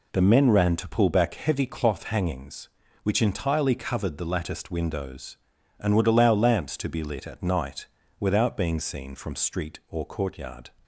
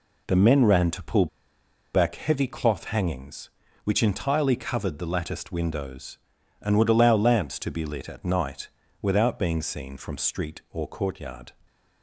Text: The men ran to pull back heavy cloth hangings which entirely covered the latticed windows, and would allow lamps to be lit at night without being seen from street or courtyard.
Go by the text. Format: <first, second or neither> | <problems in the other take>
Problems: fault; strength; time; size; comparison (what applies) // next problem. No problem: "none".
first | pauses between "pull" and "back"; noticeable; at 1.2 s; 0.68 s long // pauses between "night" and "without"; slight; at 8.6 s; 0.34 s long; slight in the first